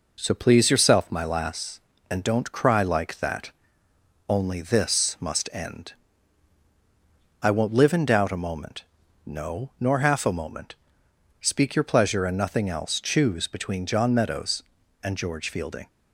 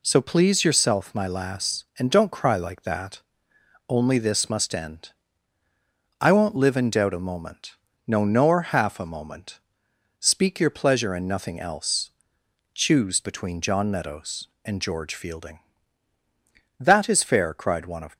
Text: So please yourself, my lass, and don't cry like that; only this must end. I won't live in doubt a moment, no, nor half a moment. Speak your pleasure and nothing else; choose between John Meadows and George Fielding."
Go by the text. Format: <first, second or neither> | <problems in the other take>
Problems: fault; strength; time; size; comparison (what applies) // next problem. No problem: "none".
first | goes on to say "That is fair cried one of"; from 16.8 s on; 1.3 s long